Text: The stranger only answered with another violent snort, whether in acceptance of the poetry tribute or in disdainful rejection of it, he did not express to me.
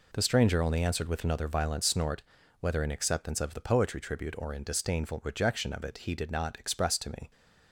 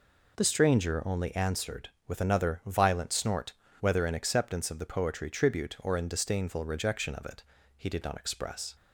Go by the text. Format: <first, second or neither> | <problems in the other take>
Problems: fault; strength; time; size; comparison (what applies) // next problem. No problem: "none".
first | stops before "to me"; at 8.7 s